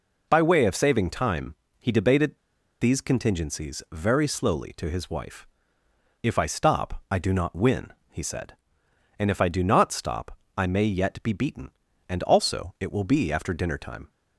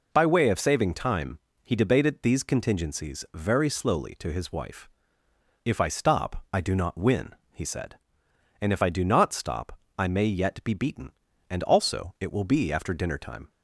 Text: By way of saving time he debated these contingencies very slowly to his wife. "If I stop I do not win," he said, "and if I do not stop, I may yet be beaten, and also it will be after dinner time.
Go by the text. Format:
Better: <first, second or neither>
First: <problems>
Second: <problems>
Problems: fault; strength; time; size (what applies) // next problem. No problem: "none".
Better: second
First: pauses between "time" and "he"; slight; at 1.5 s; 0.26 s long // pauses between "debated" and "these"; at 2.3 s; 0.41 s long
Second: pauses between "time" and "he"; slight; at 1.3 s; 0.26 s long